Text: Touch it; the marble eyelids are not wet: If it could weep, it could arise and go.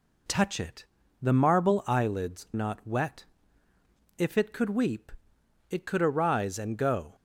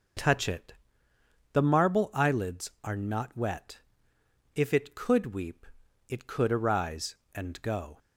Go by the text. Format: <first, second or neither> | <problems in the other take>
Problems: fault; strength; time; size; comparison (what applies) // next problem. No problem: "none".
second | skips "are"; at 2.5 s